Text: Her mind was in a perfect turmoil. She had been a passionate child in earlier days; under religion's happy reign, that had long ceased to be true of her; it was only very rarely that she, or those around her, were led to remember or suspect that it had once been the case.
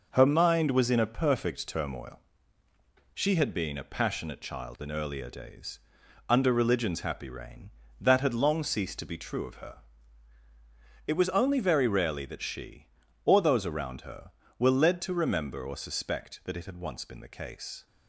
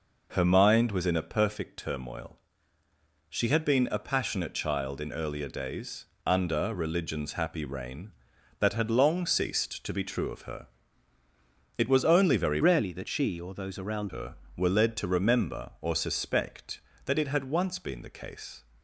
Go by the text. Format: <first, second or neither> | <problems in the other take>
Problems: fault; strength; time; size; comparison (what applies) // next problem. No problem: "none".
first | changes voice from "rarely" to "around"; from 12.6 to 14.1 s; 1.5 s long